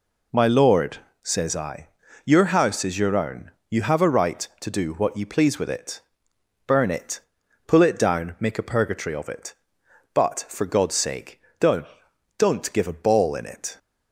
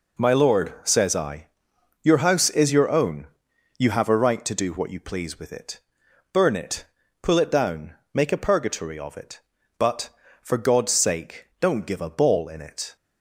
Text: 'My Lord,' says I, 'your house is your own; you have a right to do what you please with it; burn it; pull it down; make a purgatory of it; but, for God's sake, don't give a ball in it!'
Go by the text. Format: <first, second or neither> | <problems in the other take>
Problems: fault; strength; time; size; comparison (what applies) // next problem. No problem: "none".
second | says "don't" twice; at 12.3 s